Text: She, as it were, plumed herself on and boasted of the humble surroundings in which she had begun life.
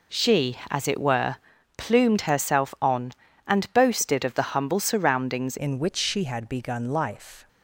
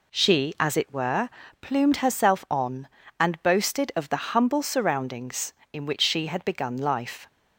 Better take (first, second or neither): second